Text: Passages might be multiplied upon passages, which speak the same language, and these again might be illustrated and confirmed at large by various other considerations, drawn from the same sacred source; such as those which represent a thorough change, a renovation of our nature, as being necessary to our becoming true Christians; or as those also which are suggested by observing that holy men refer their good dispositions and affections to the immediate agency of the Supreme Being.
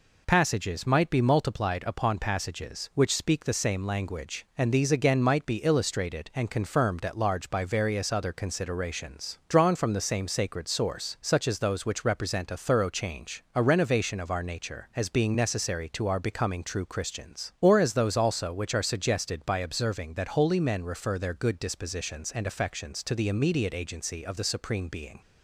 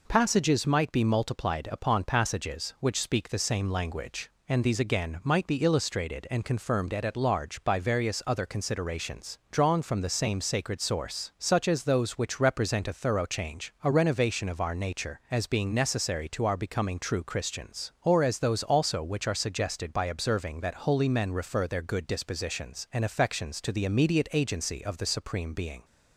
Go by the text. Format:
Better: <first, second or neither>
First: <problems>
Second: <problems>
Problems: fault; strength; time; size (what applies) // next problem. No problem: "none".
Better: first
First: none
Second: says "at" twice; at 7.0 s